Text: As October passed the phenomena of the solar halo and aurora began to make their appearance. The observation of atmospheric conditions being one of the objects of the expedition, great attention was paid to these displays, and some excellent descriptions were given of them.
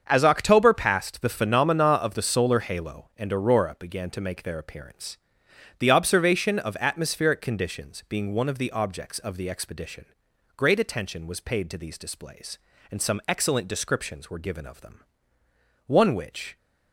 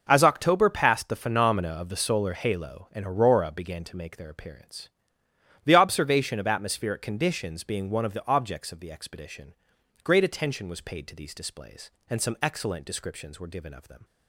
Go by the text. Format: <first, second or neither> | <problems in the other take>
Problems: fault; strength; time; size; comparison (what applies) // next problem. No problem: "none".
second | starts louder than the rest; until 1.0 s; 7 dB // goes on to say "One which"; noticeable; from 15.8 s on; 0.70 s long